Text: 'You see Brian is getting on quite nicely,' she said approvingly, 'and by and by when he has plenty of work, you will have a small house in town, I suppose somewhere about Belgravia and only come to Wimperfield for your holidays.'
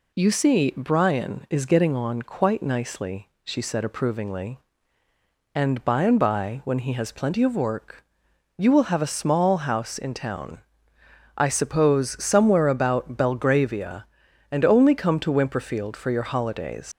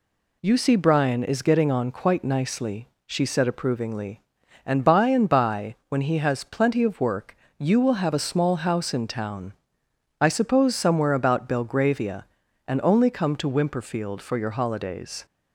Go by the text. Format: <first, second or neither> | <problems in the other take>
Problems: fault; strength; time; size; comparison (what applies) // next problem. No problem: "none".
second | leaves "holidays" unfinished; at 16.9 s; 100 ms